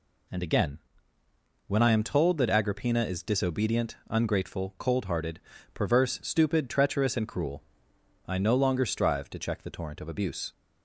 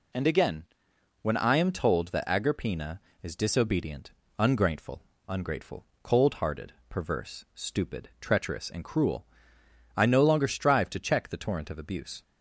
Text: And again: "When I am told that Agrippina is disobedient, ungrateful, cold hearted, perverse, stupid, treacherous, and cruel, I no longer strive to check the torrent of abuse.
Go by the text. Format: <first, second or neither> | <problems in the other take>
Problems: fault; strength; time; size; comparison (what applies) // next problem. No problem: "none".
first | says "ungrateful" twice; at 5.2 s